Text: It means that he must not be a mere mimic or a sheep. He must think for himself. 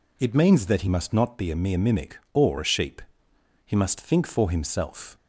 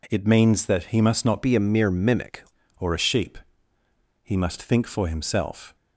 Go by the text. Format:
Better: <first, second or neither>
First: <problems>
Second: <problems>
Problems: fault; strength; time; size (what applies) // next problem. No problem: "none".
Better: first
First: none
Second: changes voice from "be" to "mimic"; from 1.4 to 2.4 s; 1.0 s long